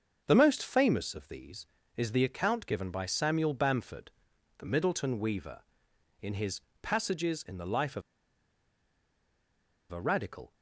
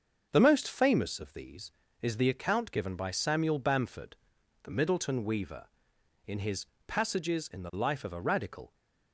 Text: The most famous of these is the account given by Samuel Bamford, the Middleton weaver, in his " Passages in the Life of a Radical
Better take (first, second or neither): second